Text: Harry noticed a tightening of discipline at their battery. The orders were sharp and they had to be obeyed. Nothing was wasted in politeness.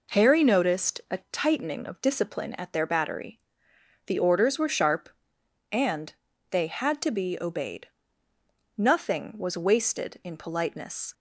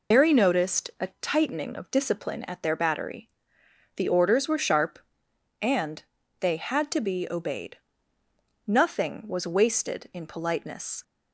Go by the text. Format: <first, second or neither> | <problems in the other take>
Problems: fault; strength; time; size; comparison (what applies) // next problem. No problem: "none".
first | loses the start of "Harry"; at 0.1 s; 120 ms // pauses between "and" and "they"; slight; at 6.0 s; 0.36 s long; slight in the first